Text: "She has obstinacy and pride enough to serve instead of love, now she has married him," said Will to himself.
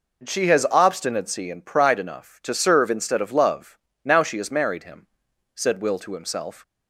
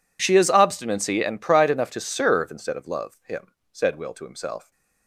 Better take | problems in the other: first | skips "now she has married"; at 3.2 s

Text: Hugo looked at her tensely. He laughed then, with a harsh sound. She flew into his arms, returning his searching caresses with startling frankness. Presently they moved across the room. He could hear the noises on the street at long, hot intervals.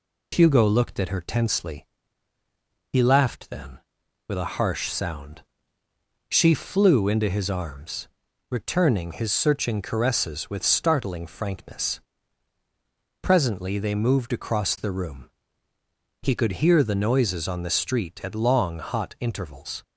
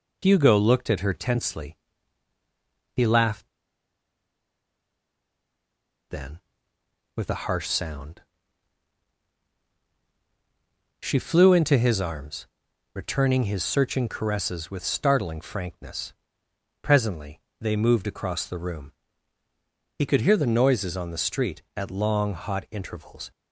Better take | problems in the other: first | pauses between "laughed" and "then"; strong; at 3.4 s; 2.6 s long // pauses between "Presently" and "they"; slight; at 17.4 s; 0.20 s long

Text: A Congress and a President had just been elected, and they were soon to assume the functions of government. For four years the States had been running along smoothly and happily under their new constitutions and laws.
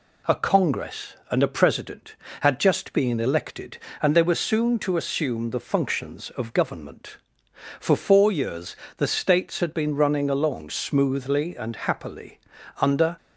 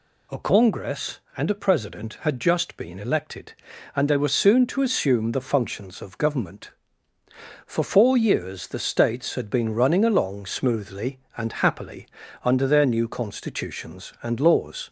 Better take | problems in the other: second | pauses between "years" and "the"; slight; at 8.7 s; 0.22 s long // pauses between "happily" and "under"; at 12.3 s; 0.42 s long; slight in the second // stops before "their new constitutions and laws"; at 13.1 s

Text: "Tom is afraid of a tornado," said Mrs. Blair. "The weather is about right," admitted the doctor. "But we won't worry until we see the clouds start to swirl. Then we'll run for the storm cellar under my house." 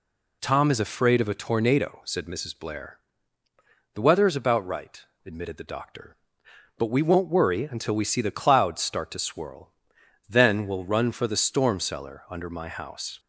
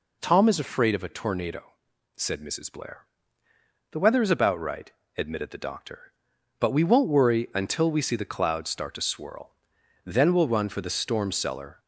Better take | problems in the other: first | stops before "under my house"; at 11.7 s

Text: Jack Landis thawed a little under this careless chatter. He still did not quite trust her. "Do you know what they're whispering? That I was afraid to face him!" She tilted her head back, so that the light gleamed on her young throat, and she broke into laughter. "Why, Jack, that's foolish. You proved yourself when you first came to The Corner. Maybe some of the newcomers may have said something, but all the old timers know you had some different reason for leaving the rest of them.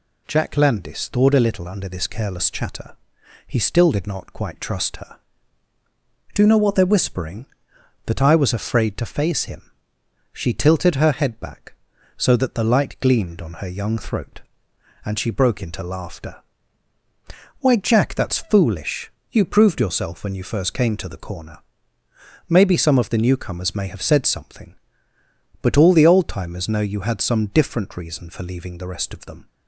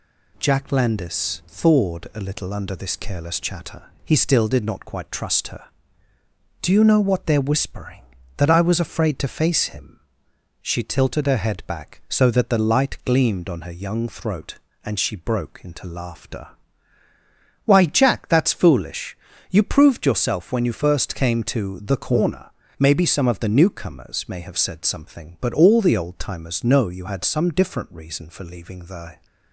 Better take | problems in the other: first | stops before "rest of them"; at 29.2 s

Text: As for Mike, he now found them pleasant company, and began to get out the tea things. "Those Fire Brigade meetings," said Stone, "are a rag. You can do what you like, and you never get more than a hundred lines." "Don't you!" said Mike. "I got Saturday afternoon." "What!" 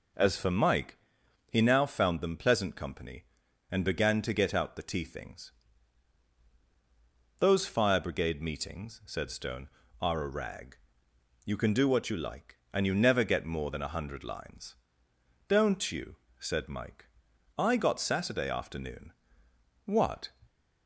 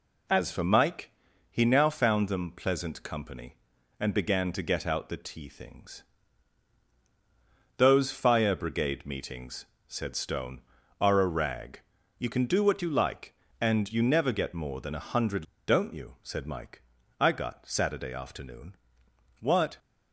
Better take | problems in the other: first | skips "lines"; at 15.5 s

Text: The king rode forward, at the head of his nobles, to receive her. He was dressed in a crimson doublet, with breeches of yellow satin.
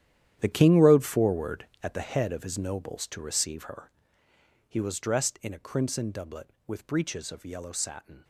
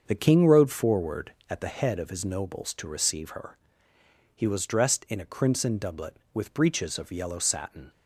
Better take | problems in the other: second | gets quieter; strong; throughout; 14 dB // starts louder than the rest; strong; until 1.4 s; 11 dB; also in the second

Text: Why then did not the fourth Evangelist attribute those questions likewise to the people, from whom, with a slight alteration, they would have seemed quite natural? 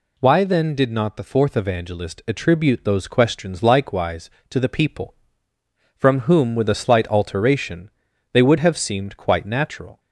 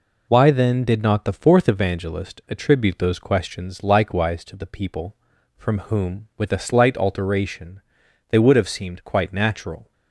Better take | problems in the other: neither | none

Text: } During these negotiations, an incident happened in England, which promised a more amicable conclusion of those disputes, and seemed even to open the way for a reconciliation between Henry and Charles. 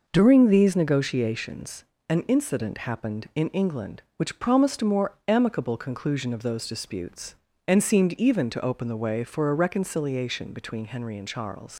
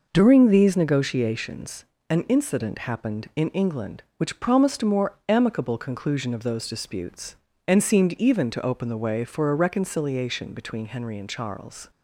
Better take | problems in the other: second | leaves "Charles" unfinished; at 11.7 s; 95 ms

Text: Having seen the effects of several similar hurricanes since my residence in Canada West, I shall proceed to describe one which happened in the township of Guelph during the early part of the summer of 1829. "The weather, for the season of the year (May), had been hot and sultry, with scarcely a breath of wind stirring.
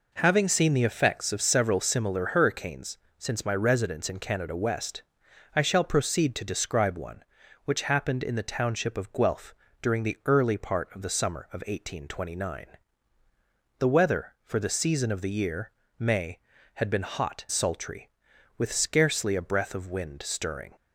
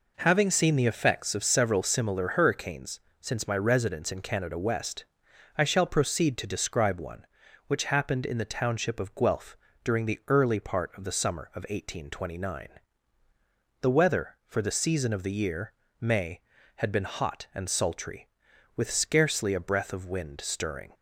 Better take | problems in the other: second | pauses between "hurricanes" and "since"; slight; at 2.9 s; 0.20 s long; slight in the second // pauses between "Guelph" and "during"; slight; at 9.5 s; 0.26 s long; slight in the second // skips "and"; at 17.4 s

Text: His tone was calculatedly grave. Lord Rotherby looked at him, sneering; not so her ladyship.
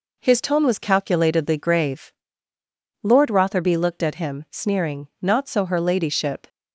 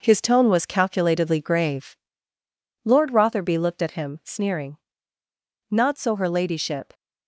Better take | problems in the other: first | gets quieter; throughout; 6.5 dB

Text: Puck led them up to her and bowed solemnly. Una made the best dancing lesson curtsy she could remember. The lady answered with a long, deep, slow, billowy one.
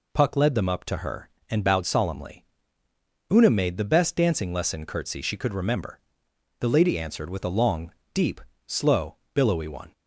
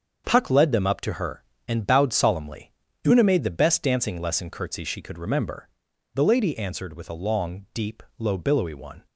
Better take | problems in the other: first | starts louder than the rest; until 1.2 s; 6.5 dB // says "low" for "slow"; at 8.1 s

